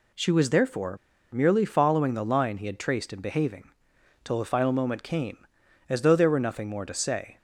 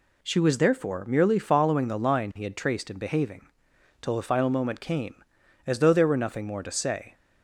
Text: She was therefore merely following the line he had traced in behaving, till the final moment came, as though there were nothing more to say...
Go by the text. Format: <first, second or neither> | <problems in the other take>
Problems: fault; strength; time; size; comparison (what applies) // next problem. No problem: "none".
second | pauses between "therefore" and "merely"; slight; at 0.9 s; 0.35 s long